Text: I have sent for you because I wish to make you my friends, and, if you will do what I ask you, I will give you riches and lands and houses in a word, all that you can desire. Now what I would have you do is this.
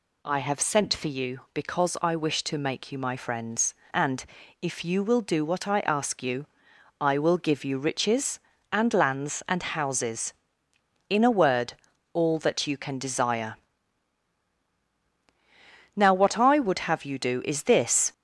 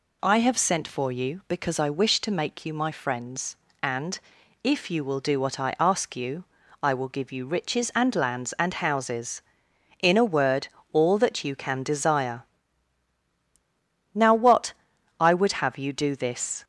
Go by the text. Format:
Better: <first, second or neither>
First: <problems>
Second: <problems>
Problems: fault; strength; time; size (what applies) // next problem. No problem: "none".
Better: first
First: none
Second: pauses between "what" and "I"; noticeable; at 14.7 s; 0.46 s long // skips "is"; at 16.1 s